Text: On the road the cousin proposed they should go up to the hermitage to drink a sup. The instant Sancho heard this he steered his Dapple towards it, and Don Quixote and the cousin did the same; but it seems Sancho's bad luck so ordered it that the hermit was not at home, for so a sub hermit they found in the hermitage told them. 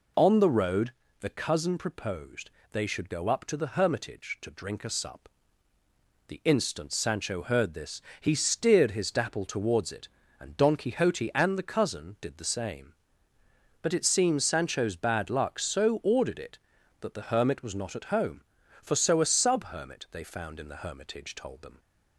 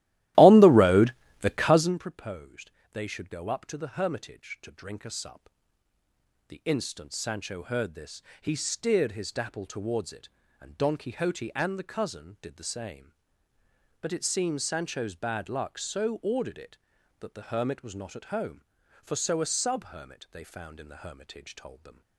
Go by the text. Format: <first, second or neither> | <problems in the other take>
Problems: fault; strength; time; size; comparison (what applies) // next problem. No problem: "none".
first | starts louder than the rest; strong; until 2.1 s; 15.5 dB // pauses between "road" and "the"; slight; at 1.1 s; 0.28 s long; slight in the first // pauses between "proposed" and "they"; slight; at 2.7 s; 0.20 s long; slight in the first // pauses between "this" and "he"; slight; at 8.2 s; 0.20 s long; slight in the first